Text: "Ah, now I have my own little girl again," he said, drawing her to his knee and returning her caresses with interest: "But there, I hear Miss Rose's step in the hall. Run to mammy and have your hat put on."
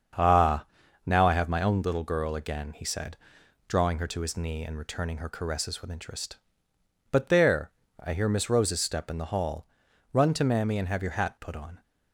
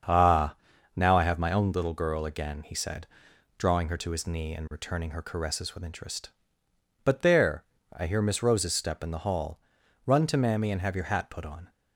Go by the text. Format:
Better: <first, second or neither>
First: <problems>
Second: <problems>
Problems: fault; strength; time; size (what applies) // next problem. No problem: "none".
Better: neither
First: starts louder than the rest; strong; until 1.5 s; 7 dB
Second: starts louder than the rest; strong; until 1.4 s; 7 dB